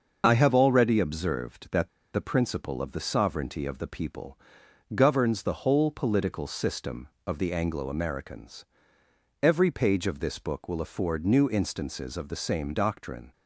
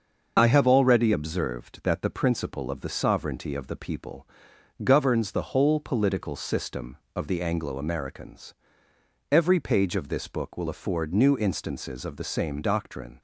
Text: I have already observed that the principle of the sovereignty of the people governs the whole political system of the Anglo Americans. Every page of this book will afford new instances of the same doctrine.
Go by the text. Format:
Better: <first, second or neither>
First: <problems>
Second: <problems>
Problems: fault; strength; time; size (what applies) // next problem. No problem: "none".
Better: second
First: starts louder than the rest; until 1.2 s; 6 dB // pauses between "that" and "the"; slight; at 1.8 s; 0.25 s long // pauses between "people" and "governs"; noticeable; at 4.3 s; 0.56 s long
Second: starts louder than the rest; noticeable; until 1.4 s; 6 dB // pauses between "people" and "governs"; noticeable; at 4.2 s; 0.56 s long